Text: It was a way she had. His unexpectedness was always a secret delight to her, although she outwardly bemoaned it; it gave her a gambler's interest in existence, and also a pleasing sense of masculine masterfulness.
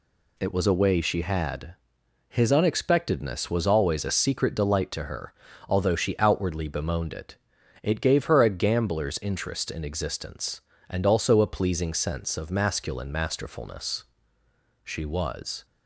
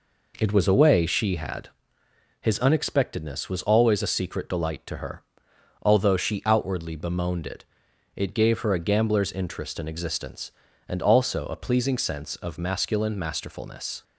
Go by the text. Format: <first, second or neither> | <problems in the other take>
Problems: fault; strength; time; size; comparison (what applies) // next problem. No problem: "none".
second | goes on to say "She was"; noticeable; from 14.8 s on; 0.80 s long